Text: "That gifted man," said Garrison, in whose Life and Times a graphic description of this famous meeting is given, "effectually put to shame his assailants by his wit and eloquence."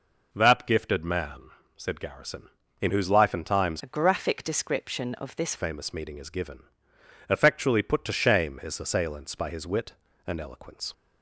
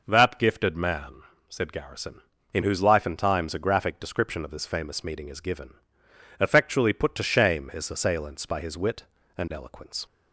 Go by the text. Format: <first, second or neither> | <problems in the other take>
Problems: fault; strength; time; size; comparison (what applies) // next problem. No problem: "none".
second | changes voice from "a" to "this"; from 3.8 to 5.5 s; 1.7 s long